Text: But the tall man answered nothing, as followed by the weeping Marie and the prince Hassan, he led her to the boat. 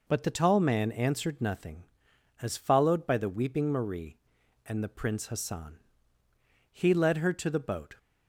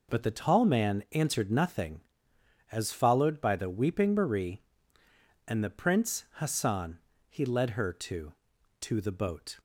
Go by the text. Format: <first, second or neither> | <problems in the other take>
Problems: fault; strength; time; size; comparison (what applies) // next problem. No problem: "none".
first | says "to" twice; at 8.8 s